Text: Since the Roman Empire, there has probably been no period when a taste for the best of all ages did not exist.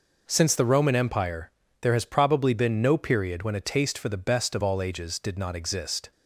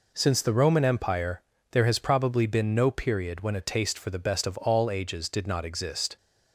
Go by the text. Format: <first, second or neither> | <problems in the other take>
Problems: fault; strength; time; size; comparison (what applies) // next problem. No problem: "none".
neither | none